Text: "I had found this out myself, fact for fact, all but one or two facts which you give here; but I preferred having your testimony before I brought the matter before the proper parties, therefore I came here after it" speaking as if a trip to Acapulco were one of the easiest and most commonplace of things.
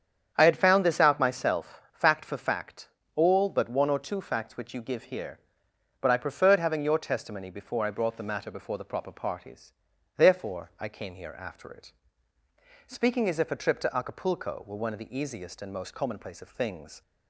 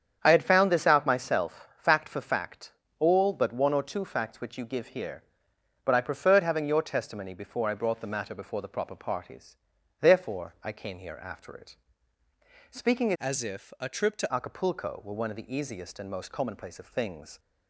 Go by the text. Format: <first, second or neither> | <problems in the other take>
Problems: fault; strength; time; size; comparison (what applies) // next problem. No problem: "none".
first | starts louder than the rest; strong; until 1.2 s; 8 dB; strong in the first // pauses between "it" and "speaking"; noticeable; at 11.7 s; 0.92 s long; noticeable in the first // changes voice from "as" to "to"; from 13.1 to 14.3 s; 1.2 s long